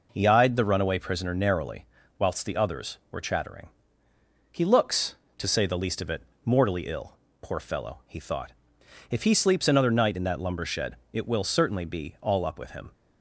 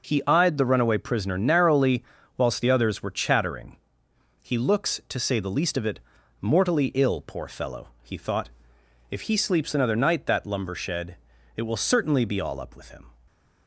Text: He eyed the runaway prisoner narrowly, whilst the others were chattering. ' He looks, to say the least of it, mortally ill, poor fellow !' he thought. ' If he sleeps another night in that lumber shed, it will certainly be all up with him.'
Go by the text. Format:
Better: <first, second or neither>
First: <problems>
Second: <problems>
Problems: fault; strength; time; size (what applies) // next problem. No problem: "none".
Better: first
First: none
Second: starts louder than the rest; until 1.1 s; 7 dB // skips "in"; at 10.2 s